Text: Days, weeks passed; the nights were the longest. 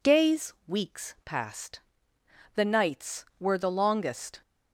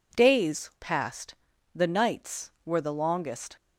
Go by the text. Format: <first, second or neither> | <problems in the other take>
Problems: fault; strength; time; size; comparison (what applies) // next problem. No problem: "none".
first | skips "weeks"; at 0.7 s